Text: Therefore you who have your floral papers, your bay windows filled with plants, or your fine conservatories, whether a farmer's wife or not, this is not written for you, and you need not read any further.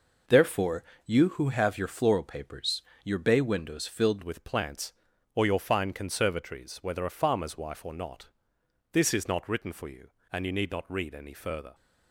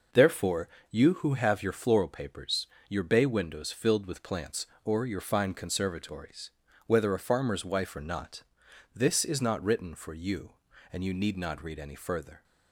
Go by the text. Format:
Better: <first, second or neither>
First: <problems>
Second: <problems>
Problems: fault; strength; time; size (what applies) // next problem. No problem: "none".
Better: second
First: pauses between "Therefore" and "you"; slight; at 0.8 s; 0.22 s long // changes voice at "with"; from 4.2 s on; 7.5 s long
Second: pauses between "Therefore" and "you"; slight; at 0.6 s; 0.22 s long